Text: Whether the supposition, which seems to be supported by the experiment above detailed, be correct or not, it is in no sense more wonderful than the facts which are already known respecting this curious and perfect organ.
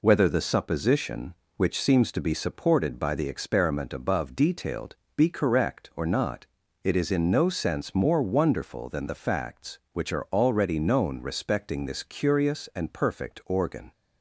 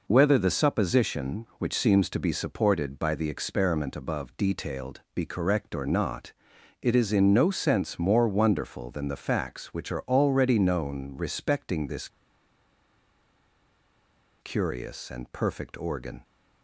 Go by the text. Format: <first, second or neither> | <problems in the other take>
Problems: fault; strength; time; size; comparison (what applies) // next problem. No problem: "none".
first | pauses between "this" and "curious"; strong; at 12.0 s; 2.3 s long